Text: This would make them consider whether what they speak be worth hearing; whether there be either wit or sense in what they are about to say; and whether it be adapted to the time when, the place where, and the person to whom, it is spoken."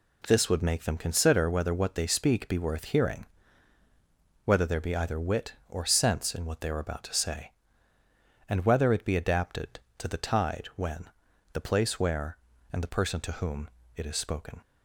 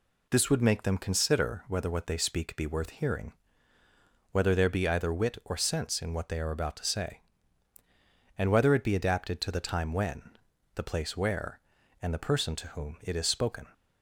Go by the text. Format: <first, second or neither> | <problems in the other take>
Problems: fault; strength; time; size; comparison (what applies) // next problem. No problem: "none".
second | says "tide" for "time"; at 10.1 s